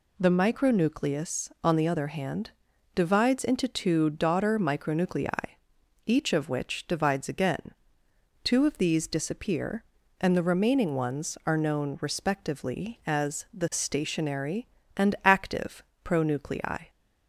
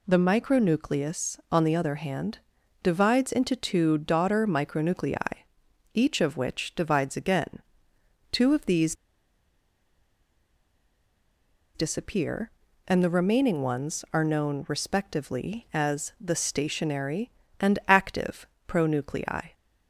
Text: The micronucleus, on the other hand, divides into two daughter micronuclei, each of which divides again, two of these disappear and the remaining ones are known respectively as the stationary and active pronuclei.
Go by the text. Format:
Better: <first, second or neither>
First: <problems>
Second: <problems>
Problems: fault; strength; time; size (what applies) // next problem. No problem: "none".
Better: first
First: pauses between "active" and "pronuclei"; slight; at 15.8 s; 0.22 s long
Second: pauses between "these" and "disappear"; strong; at 8.9 s; 2.8 s long // pauses between "active" and "pronuclei"; slight; at 18.4 s; 0.22 s long